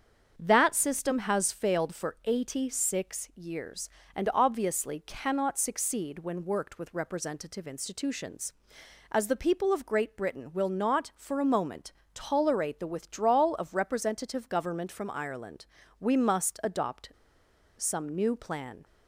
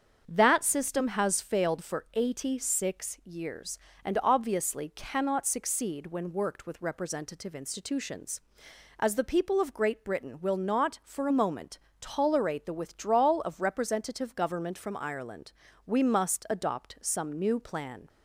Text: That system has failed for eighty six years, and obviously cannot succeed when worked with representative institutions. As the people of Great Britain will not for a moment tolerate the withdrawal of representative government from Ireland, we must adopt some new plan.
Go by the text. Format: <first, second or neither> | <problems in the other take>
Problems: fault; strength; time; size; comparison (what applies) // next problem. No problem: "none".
second | starts louder than the rest; strong; until 1.3 s; 7 dB; strong in the second // pauses between "moment" and "tolerate"; slight; at 11.9 s; 0.22 s long; slight in the second // pauses between "adopt" and "some"; noticeable; at 17.1 s; 0.66 s long